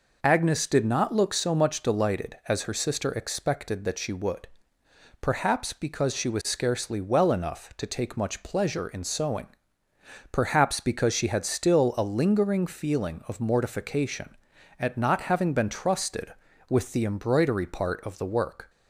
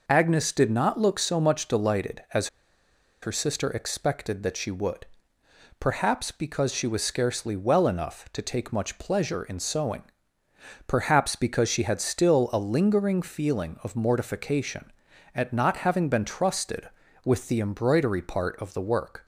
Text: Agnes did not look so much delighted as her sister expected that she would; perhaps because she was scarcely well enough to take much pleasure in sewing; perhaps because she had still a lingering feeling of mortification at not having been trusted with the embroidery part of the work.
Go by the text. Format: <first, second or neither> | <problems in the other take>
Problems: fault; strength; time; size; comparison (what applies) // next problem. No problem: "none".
first | pauses between "as" and "her"; noticeable; at 2.4 s; 0.74 s long